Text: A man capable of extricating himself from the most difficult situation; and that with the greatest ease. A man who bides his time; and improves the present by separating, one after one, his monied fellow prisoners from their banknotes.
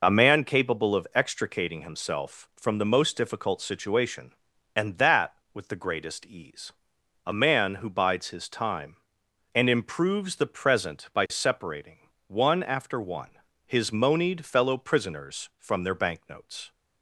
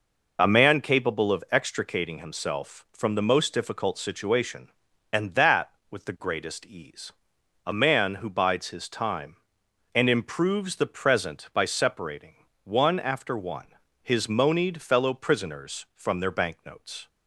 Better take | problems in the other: neither | none

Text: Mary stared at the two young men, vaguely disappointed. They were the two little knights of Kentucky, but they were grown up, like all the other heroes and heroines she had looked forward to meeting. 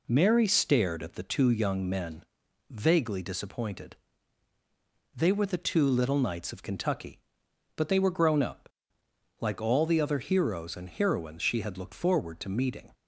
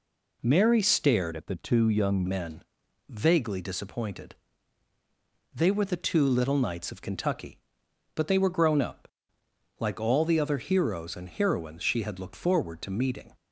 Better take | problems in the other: first | changes voice from "at" to "young"; from 1.3 to 2.2 s; 0.9 s long

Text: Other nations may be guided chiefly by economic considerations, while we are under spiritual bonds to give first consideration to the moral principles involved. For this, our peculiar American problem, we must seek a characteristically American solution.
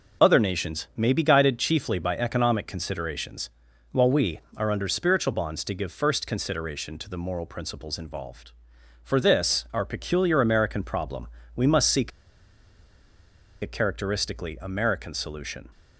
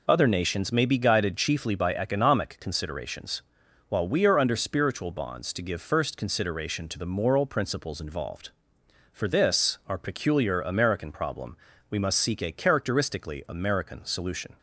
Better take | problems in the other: second | pauses between "seek" and "a"; strong; at 12.1 s; 1.5 s long

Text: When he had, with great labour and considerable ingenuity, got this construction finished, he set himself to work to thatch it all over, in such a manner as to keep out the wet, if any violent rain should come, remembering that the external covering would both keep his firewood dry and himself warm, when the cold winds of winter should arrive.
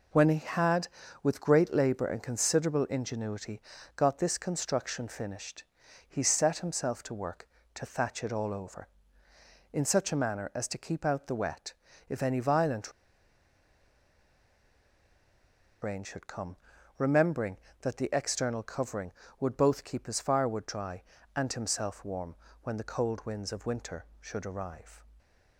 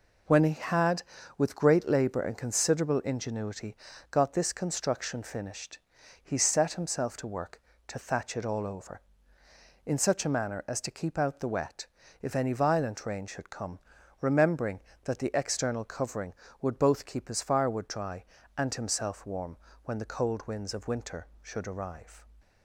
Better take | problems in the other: second | pauses between "violent" and "rain"; strong; at 12.9 s; 2.9 s long

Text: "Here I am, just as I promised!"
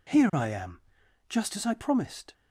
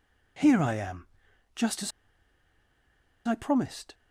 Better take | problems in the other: first | pauses between "as" and "I"; strong; at 1.9 s; 1.3 s long

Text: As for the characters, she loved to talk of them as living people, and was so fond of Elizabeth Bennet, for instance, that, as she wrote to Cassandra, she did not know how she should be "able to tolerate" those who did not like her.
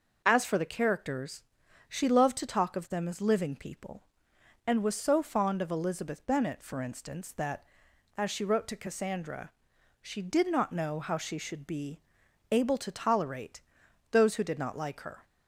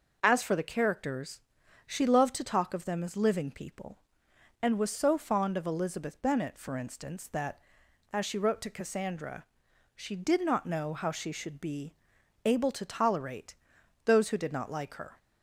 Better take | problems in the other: neither | pauses between "be" and "able"; noticeable; the same in both // pauses between "tolerate" and "those"; noticeable; the same in both

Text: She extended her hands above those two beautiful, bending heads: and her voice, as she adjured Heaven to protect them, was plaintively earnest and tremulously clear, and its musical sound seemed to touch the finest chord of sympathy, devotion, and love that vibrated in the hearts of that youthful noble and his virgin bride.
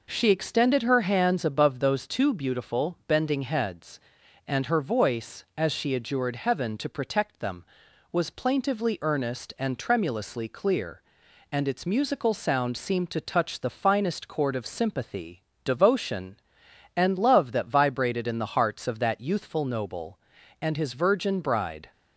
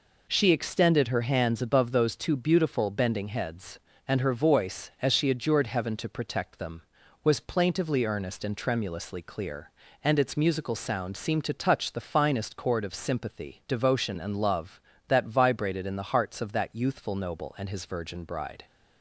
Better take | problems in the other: neither | none

